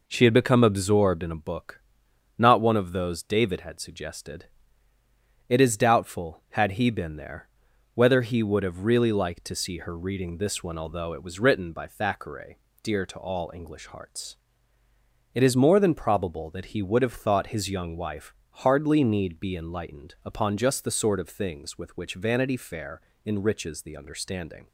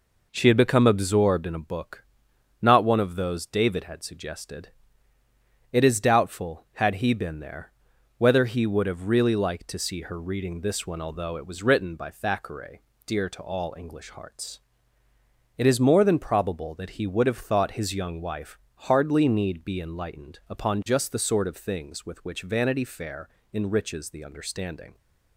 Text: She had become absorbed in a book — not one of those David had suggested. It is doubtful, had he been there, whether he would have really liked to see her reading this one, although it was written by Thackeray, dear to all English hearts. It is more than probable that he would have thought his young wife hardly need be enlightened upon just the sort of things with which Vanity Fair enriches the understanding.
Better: neither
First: pauses between "wife" and "hardly"; slight; at 18.3 s; 0.22 s long // pauses between "Fair" and "enriches"; slight; at 23.0 s; 0.24 s long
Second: pauses between "wife" and "hardly"; slight; at 18.5 s; 0.22 s long // pauses between "Fair" and "enriches"; slight; at 23.2 s; 0.24 s long

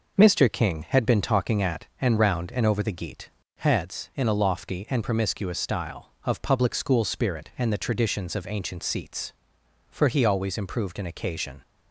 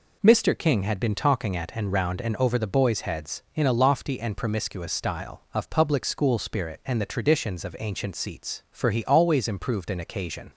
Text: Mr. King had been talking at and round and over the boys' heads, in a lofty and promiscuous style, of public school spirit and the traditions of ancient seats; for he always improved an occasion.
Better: second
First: says "geat" for "boys"; at 2.9 s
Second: none

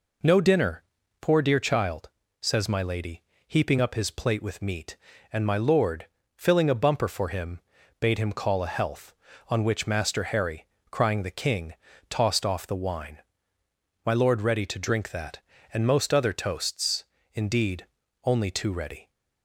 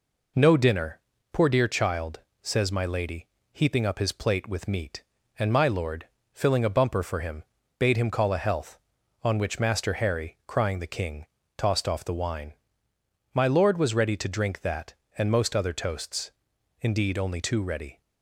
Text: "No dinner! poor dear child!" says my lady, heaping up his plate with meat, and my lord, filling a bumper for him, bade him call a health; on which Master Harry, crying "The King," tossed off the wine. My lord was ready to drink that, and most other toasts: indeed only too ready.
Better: second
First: skips "was"; at 14.4 s // pauses between "indeed" and "only"; at 17.8 s; 0.40 s long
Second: none

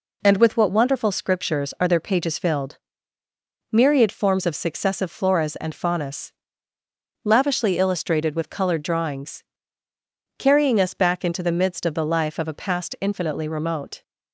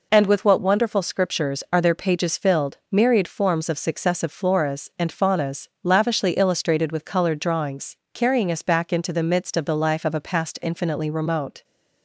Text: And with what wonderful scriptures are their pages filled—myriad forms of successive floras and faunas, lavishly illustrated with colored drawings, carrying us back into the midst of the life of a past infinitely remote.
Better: neither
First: none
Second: none

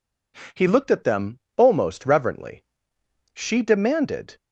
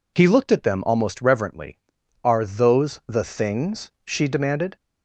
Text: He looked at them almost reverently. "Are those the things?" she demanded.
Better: second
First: pauses between "them" and "almost"; slight; at 1.3 s; 0.18 s long // skips "Are those the things"; at 2.9 s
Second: none

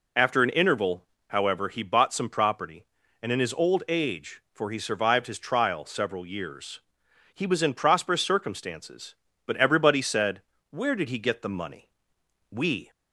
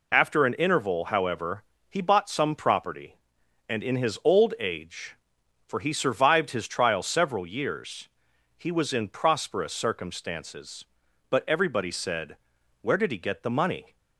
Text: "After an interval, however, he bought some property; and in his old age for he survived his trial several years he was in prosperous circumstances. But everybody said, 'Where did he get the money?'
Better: second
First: pauses between "years" and "he"; noticeable; at 6.7 s; 0.52 s long // goes on to say "We"; slight; from 12.4 s on; 0.40 s long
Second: pauses between "years" and "he"; noticeable; at 8.0 s; 0.50 s long

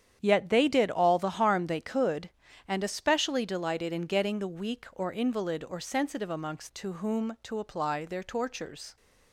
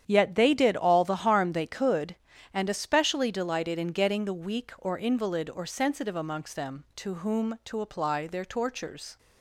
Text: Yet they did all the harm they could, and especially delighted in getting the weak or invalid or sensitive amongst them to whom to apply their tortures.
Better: second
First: starts louder than the rest; strong; until 1.2 s; 9 dB // skips "them"; at 6.7 s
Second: starts louder than the rest; strong; until 1.0 s; 9 dB

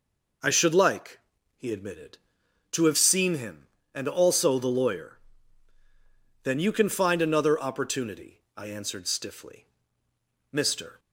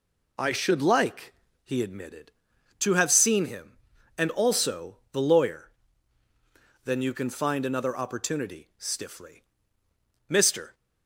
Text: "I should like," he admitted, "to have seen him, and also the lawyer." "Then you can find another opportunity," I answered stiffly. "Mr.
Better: first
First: none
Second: skips "I answered"; at 8.7 s

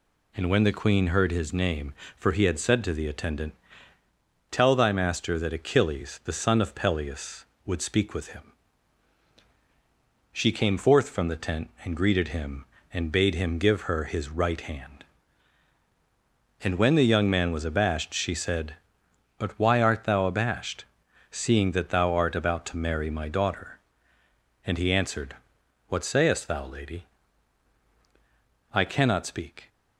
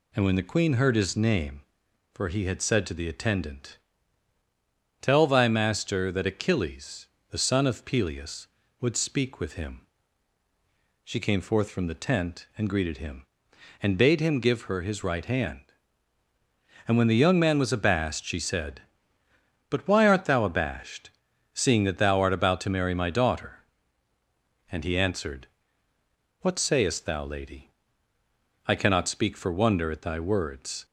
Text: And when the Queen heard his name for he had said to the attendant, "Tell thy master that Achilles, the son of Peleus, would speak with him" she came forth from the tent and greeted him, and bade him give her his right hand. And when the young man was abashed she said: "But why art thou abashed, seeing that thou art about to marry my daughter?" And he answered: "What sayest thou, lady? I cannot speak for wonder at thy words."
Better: second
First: pauses between "him" and "she"; strong; at 8.5 s; 1.8 s long // stops before "for wonder at thy words"; at 29.6 s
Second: pauses between "him" and "she"; at 9.8 s; 1.1 s long

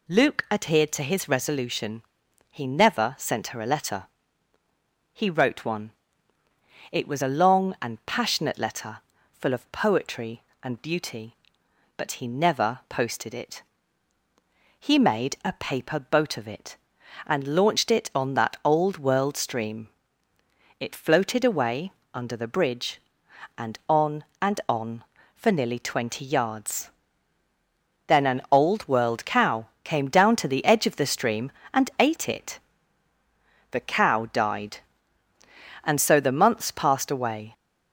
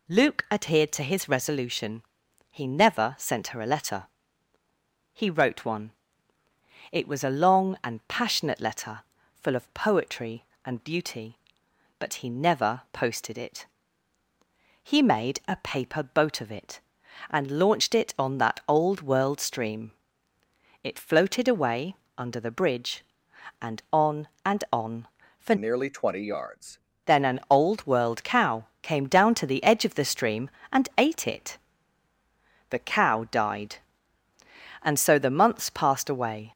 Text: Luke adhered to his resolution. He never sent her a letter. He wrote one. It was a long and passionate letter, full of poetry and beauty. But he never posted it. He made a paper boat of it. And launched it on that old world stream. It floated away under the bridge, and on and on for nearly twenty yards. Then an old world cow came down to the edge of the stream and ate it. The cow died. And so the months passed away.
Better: first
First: pauses between "away" and "under"; slight; at 21.9 s; 0.20 s long // pauses between "cow" and "came"; slight; at 29.6 s; 0.16 s long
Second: pauses between "away" and "under"; slight; at 21.9 s; 0.20 s long // changes voice from "nearly" to "yards"; from 25.5 to 26.7 s; 1.2 s long // pauses between "cow" and "came"; slight; at 28.6 s; 0.16 s long

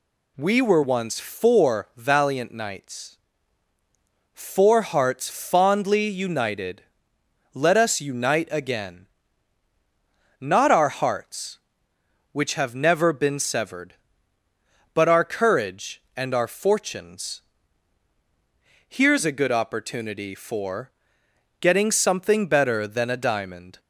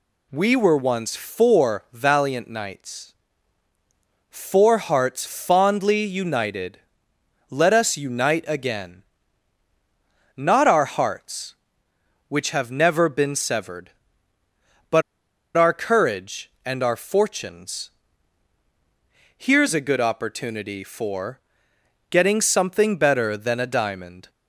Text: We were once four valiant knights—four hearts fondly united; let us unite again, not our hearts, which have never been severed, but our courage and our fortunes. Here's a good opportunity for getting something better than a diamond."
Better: first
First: pauses between "for" and "getting"; noticeable; at 20.9 s; 0.67 s long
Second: pauses between "but" and "our"; noticeable; at 15.0 s; 0.55 s long // pauses between "for" and "getting"; noticeable; at 21.4 s; 0.68 s long

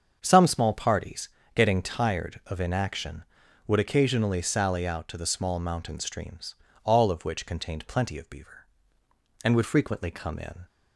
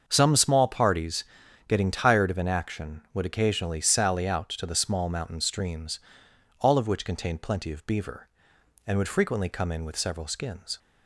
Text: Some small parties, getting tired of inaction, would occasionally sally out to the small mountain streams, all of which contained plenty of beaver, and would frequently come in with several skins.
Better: second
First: starts louder than the rest; until 1.2 s; 7 dB // stops before "with several skins"; at 10.6 s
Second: starts louder than the rest; until 1.0 s; 6.5 dB

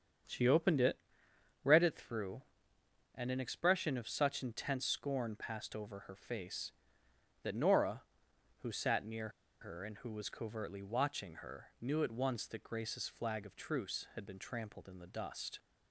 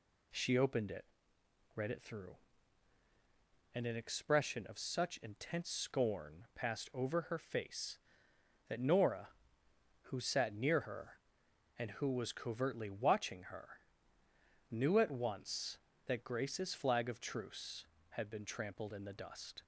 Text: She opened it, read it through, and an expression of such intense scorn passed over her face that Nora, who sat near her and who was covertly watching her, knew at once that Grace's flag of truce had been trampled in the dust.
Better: second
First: starts louder than the rest; strong; until 1.9 s; 7.5 dB // pauses between "near" and "her"; slight; at 9.2 s; 0.32 s long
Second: none

